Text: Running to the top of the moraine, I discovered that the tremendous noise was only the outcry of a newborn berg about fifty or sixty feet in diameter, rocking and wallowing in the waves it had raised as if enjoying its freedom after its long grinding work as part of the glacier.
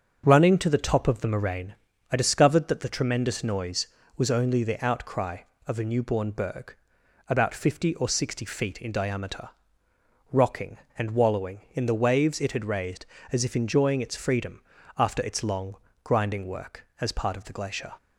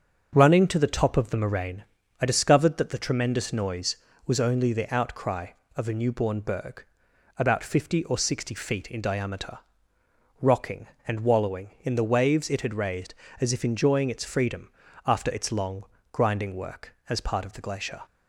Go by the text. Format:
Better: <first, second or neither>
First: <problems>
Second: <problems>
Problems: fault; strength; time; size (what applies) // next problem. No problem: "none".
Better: neither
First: starts louder than the rest; until 1.2 s; 6.5 dB // pauses between "berg" and "about"; noticeable; at 6.7 s; 0.54 s long // pauses between "freedom" and "after"; slight; at 14.6 s; 0.36 s long // pauses between "long" and "grinding"; slight; at 15.7 s; 0.28 s long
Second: starts louder than the rest; until 1.3 s; 6.5 dB // pauses between "berg" and "about"; noticeable; at 6.8 s; 0.54 s long // pauses between "freedom" and "after"; slight; at 14.7 s; 0.36 s long // pauses between "long" and "grinding"; slight; at 15.8 s; 0.28 s long